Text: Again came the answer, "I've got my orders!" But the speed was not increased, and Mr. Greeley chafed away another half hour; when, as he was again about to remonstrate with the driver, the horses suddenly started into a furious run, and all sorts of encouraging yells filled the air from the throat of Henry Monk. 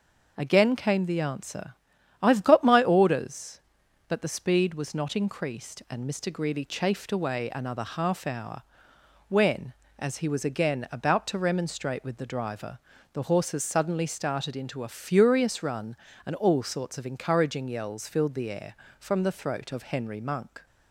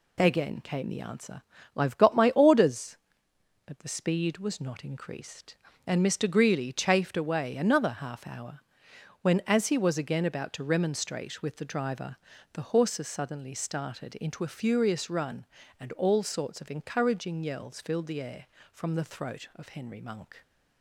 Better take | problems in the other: neither | none

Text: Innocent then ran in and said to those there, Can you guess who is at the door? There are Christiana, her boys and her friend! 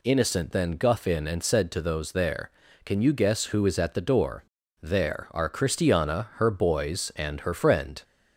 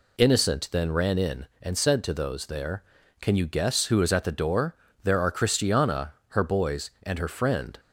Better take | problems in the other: second | says "guff" for "ran"; at 0.7 s

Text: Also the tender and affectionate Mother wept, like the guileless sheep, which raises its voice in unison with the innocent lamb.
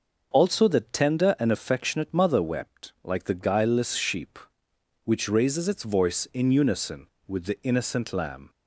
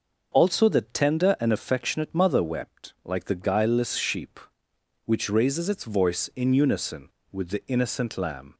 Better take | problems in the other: neither | none

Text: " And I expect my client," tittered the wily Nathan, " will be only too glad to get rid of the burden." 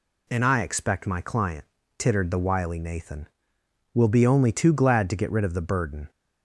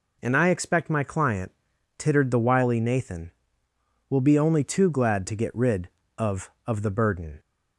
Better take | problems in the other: first | says "of" twice; at 6.6 s

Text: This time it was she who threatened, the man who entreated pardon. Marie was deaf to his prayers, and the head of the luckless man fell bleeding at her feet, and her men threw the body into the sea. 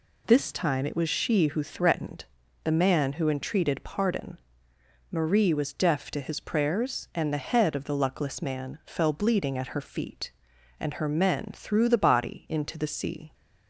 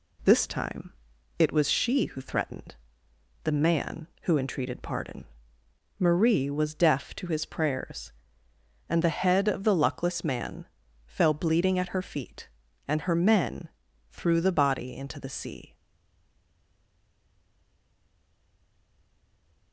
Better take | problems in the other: first | pauses between "time" and "it"; noticeable; at 0.9 s; 0.46 s long // pauses between "man" and "fell"; at 10.6 s; 0.40 s long // pauses between "men" and "threw"; at 13.6 s; 0.42 s long // stays silent after the last word; strong; from 15.7 s on; 4.0 s long

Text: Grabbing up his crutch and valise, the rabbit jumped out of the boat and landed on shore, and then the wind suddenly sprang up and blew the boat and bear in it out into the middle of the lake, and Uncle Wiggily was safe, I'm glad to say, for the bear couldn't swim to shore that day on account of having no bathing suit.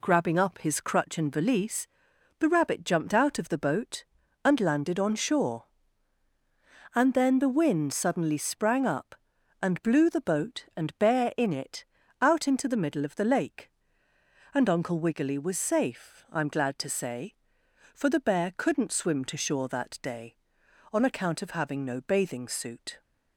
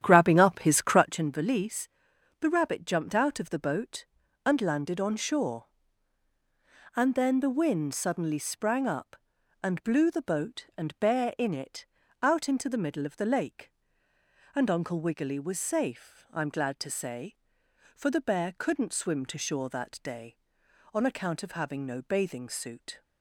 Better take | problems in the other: first | starts louder than the rest; strong; until 1.3 s; 10.5 dB // pauses between "it" and "out"; slight; at 11.8 s; 0.34 s long; slight in the first

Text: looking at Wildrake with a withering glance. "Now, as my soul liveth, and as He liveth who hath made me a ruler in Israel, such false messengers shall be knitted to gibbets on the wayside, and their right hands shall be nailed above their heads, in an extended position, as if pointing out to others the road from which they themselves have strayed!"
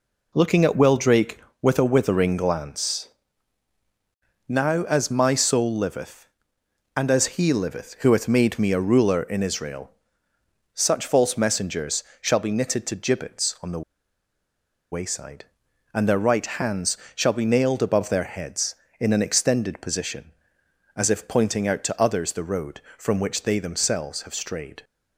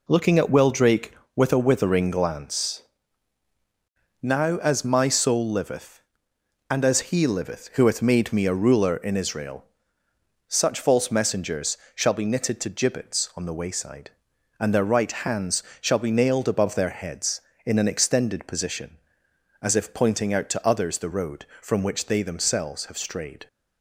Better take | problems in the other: second | pauses between "messengers" and "shall"; slight; at 12.0 s; 0.18 s long; slight in the second // pauses between "the" and "wayside"; at 13.8 s; 1.1 s long // pauses between "hands" and "shall"; slight; at 16.9 s; 0.20 s long; slight in the second

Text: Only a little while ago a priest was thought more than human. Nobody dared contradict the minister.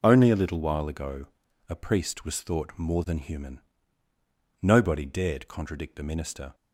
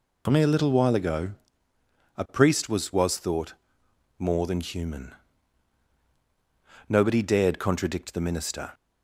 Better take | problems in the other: first | pauses between "ago" and "a"; noticeable; at 1.3 s; 0.86 s long; also in the first // says "was" twice; at 2.9 s // pauses between "thought" and "more"; noticeable; at 3.5 s; 0.64 s long

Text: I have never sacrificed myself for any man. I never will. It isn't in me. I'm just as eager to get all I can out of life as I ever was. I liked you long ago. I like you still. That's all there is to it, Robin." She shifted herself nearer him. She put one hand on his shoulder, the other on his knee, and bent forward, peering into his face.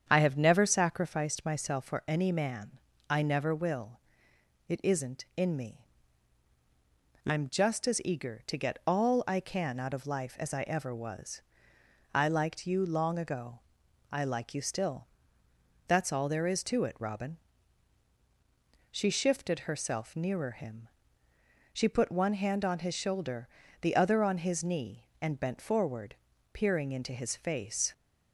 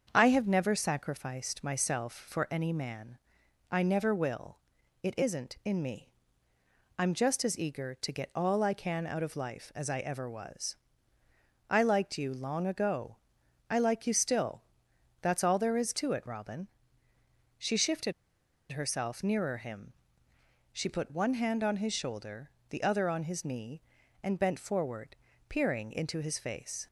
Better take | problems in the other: first | starts louder than the rest; until 1.1 s; 7 dB; strong in the first // pauses between "shifted" and "herself"; noticeable; at 18.1 s; 0.58 s long

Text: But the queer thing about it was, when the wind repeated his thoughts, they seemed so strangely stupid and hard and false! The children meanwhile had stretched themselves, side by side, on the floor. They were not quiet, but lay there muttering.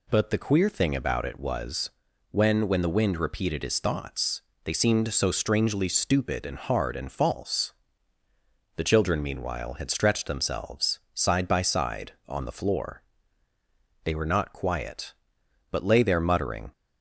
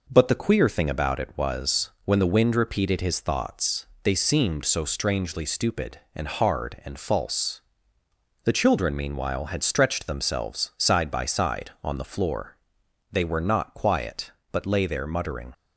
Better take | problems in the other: second | says "when" twice; at 2.6 s

